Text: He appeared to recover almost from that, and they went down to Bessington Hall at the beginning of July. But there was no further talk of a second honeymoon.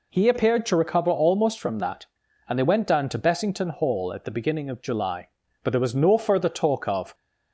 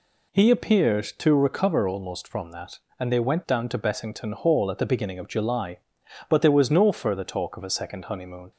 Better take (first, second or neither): second